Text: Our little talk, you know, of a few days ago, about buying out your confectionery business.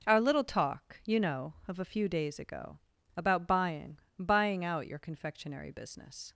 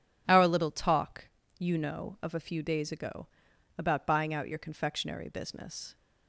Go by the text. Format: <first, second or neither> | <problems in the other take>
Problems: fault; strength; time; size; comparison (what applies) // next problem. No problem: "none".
second | says "buying" twice; at 4.1 s